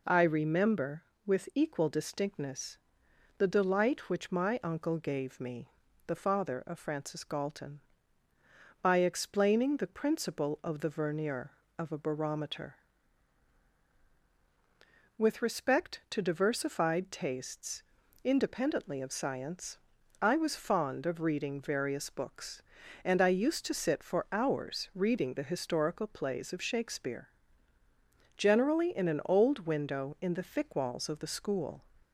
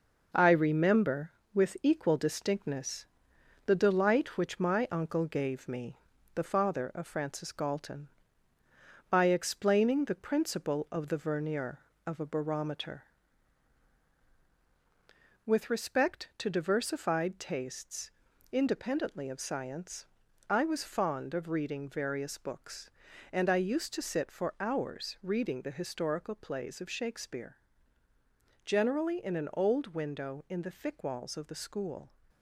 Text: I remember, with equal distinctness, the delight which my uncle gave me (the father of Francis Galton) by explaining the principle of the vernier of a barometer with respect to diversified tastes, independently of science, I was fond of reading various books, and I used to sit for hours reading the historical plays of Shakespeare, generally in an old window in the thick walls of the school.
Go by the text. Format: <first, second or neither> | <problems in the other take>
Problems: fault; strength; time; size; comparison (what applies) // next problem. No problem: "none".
first | gets quieter; noticeable; throughout; 5.5 dB